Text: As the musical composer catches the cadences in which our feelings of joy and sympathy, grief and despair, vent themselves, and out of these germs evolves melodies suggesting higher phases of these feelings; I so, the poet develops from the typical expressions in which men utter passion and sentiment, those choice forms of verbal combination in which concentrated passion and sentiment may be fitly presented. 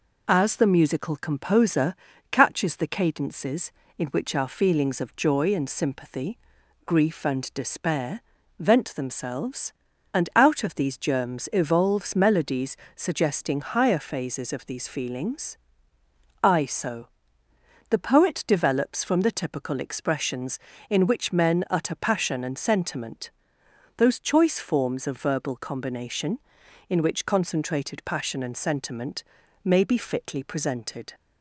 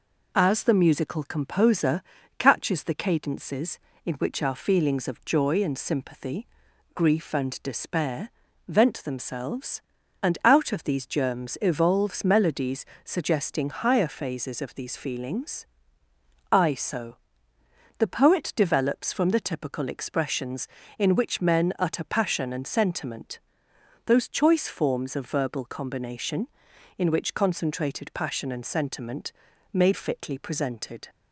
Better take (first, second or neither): first